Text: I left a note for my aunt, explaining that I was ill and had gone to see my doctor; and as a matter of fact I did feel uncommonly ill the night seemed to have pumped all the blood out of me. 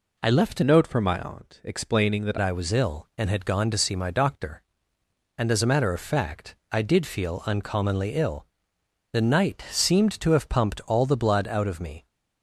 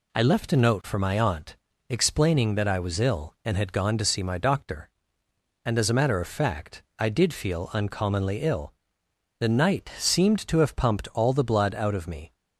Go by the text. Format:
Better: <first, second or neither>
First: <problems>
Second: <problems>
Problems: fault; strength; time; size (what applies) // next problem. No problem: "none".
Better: second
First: changes voice from "note" to "that"; from 0.6 to 2.3 s; 1.7 s long // pauses between "fact" and "I"; slight; at 6.5 s; 0.16 s long // pauses between "ill" and "the"; noticeable; at 8.4 s; 0.66 s long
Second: pauses between "fact" and "I"; slight; at 6.8 s; 0.16 s long // pauses between "ill" and "the"; noticeable; at 8.7 s; 0.66 s long